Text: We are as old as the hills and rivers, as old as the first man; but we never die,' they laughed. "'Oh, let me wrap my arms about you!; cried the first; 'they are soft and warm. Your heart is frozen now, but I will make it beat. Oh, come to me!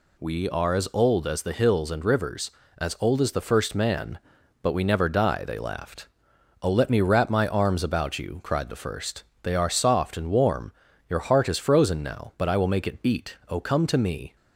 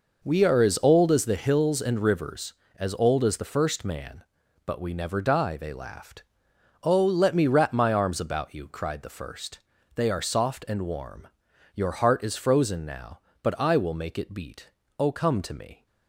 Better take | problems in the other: first | starts louder than the rest; noticeable; until 1.3 s; 5 dB

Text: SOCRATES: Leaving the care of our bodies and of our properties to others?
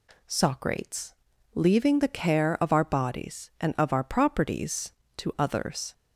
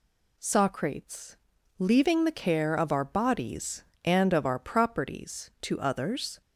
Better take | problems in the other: neither | none

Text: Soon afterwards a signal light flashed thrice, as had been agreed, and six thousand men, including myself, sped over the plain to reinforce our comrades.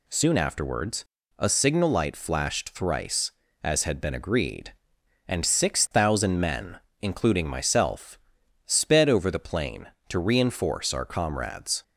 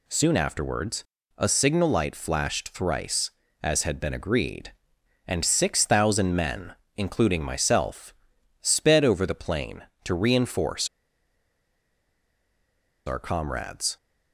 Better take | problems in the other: first | pauses between "afterwards" and "a"; slight; at 1.0 s; 0.34 s long; slight in the first // pauses between "reinforce" and "our"; strong; at 10.8 s; 2.1 s long

